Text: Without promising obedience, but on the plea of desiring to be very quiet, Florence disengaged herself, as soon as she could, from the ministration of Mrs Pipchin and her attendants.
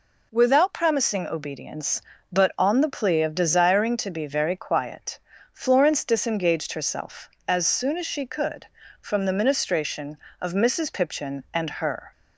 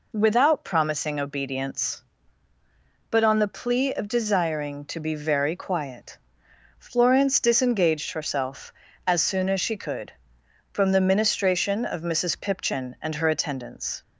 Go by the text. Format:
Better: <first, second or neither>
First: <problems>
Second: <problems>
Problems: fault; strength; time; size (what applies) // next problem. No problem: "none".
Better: second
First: stops before "attendants"; at 12.1 s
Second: none